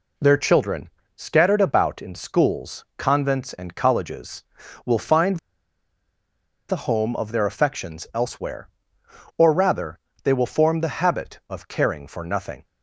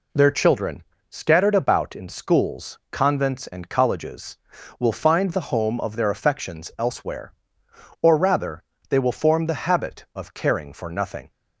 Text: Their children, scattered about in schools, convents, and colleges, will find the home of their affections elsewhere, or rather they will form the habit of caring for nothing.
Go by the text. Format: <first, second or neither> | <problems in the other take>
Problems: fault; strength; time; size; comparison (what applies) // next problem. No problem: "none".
second | pauses between "find" and "the"; strong; at 5.3 s; 1.3 s long // pauses between "rather" and "they"; slight; at 9.9 s; 0.24 s long; slight in the second